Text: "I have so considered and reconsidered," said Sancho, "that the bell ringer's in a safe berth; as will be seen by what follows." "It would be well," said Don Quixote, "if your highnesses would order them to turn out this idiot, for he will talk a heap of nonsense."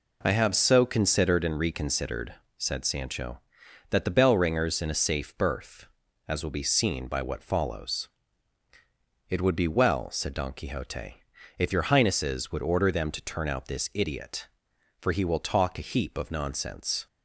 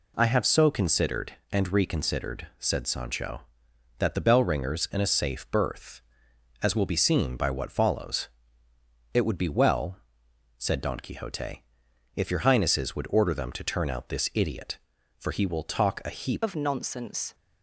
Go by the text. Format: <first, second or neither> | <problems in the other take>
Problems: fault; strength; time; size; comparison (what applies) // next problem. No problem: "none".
first | changes voice at "of"; from 16.4 s on; 0.9 s long